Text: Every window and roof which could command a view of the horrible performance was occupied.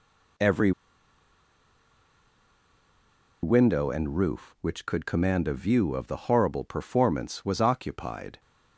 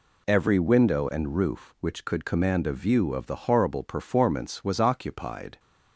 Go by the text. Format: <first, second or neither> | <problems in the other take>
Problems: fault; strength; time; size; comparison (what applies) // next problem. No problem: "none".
second | pauses between "Every" and "window"; strong; at 0.7 s; 2.7 s long